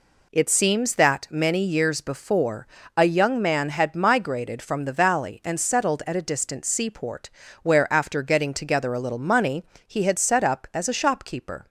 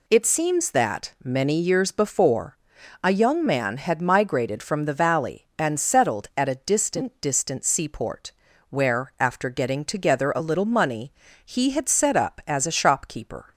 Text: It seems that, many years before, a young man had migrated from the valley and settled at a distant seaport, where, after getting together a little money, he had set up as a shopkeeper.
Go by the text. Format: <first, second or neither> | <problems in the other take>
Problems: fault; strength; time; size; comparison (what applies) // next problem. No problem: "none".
first | says "distant" twice; at 7.2 s